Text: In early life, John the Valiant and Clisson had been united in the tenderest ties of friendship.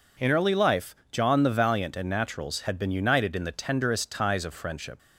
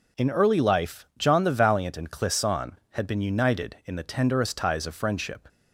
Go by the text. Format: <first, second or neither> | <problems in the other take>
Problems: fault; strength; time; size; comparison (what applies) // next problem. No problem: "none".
second | says "Naturals" for "Clisson"; at 2.0 s